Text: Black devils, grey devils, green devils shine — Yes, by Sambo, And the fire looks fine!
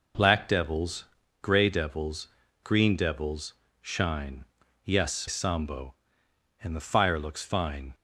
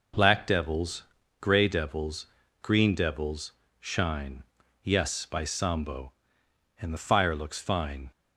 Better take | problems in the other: second | pauses between "devils" and "shine"; slight; at 3.5 s; 0.30 s long; slight in the second // skips "by"; at 5.2 s

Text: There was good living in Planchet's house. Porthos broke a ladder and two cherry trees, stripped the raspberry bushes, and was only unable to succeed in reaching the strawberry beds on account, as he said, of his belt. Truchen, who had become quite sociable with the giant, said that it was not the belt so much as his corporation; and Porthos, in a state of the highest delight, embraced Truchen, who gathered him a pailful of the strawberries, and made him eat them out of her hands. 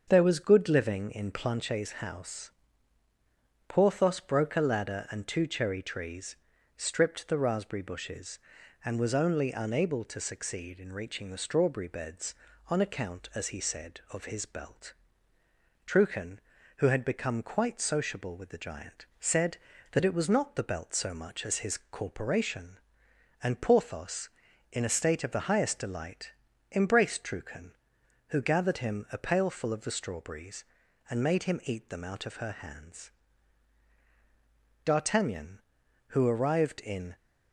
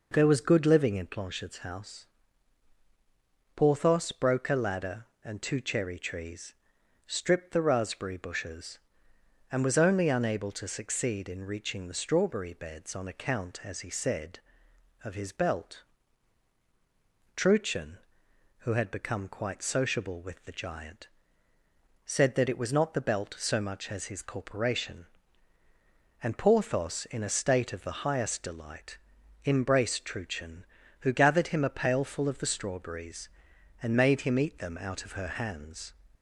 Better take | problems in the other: second | starts louder than the rest; until 1.0 s; 7 dB // goes on to say "D'Artagnan who arrived in"; strong; from 34.8 s on; 2.3 s long

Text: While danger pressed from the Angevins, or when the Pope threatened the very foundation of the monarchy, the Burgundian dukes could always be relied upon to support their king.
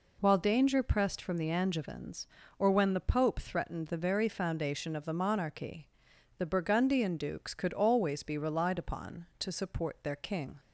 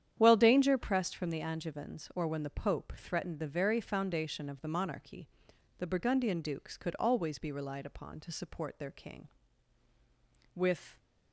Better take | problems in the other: first | starts louder than the rest; strong; until 1.1 s; 9.5 dB // goes on to say "With"; slight; from 10.5 s on; 0.42 s long

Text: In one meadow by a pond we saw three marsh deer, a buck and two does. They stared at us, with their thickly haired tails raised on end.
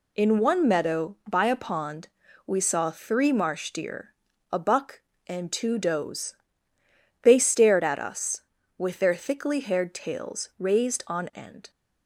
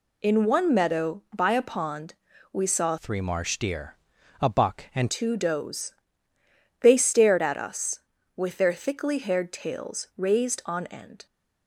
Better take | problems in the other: first | pauses between "pond" and "we"; at 2.1 s; 0.38 s long; also in the first // changes voice from "three" to "and"; from 2.9 to 5.1 s; 2.2 s long

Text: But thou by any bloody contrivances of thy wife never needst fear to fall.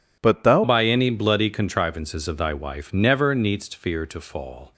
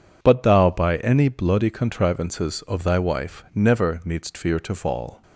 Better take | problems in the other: second | changes voice at "by"; from 0.6 s on; 4.1 s long

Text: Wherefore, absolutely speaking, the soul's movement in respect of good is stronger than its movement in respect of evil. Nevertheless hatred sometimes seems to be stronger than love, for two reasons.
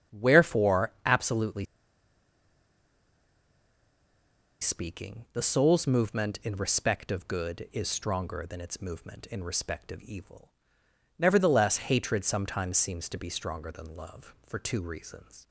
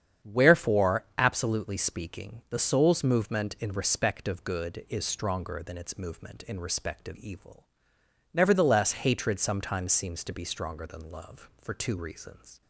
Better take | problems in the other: second | starts louder than the rest; strong; until 1.2 s; 8.5 dB; strong in the second // pauses between "absolutely" and "speaking"; strong; at 1.6 s; 2.9 s long

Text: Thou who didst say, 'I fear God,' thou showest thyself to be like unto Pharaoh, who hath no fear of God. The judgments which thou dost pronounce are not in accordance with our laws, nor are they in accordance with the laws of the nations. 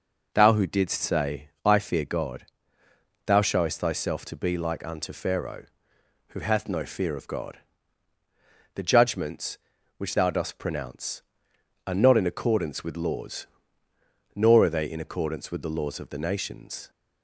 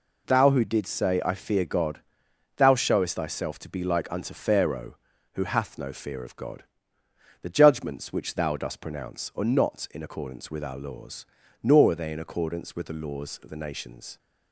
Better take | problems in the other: second | skips "our"; at 12.9 s

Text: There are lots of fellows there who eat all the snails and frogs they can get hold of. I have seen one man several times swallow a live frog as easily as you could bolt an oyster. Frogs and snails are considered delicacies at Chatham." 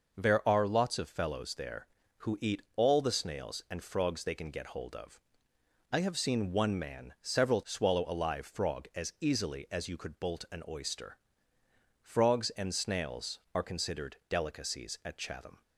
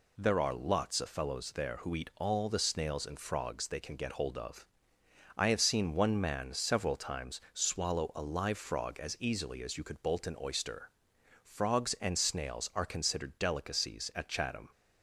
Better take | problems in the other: second | skips "times"; at 7.6 s

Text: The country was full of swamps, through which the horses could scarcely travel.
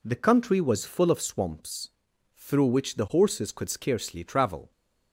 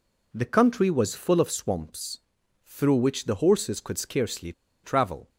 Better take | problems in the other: first | pauses between "scarcely" and "travel"; slight; at 4.5 s; 0.32 s long

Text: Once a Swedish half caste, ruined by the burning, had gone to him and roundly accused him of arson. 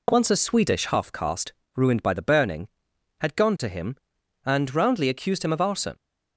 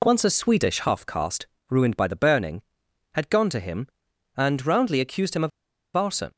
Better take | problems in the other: first | pauses between "of" and "arson"; noticeable; at 5.5 s; 0.47 s long

